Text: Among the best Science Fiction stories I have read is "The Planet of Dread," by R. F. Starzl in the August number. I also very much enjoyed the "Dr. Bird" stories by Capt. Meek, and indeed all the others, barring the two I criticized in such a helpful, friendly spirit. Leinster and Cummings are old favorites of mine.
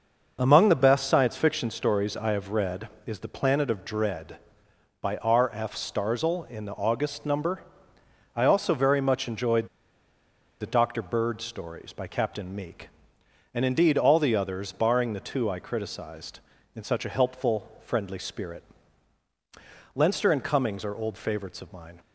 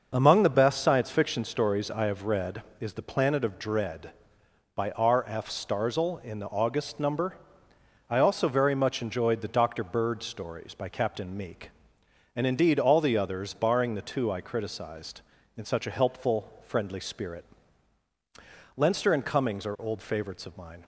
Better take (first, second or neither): second